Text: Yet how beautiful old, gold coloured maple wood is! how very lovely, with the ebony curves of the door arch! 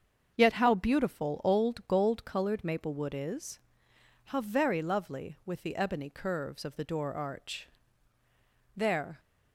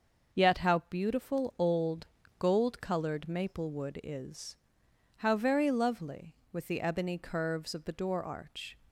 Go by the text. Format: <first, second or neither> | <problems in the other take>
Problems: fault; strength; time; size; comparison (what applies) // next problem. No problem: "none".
second | starts louder than the rest; until 1.3 s; 7 dB; also in the second // goes on to say "There"; slight; from 8.7 s on; 0.42 s long